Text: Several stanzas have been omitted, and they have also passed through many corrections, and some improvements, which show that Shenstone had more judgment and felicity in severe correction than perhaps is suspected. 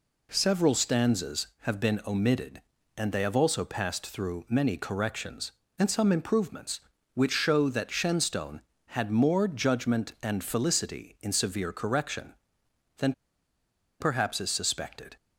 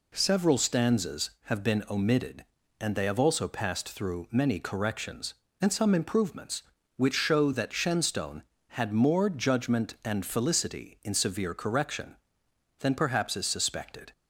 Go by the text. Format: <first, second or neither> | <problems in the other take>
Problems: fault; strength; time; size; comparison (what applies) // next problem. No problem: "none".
second | pauses between "than" and "perhaps"; noticeable; at 13.1 s; 0.88 s long